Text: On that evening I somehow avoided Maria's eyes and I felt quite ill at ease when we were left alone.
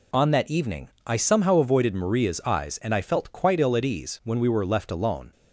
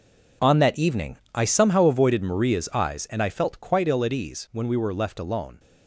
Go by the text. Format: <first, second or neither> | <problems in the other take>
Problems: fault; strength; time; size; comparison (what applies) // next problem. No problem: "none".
first | gets quieter; strong; throughout; 12.5 dB // pauses between "evening" and "I"; slight; at 1.1 s; 0.16 s long; slight in the first